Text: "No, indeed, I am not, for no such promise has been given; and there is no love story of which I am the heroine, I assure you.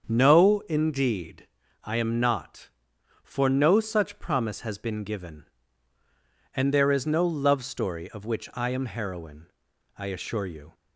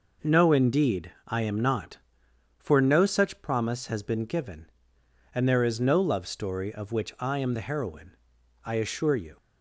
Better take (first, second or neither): second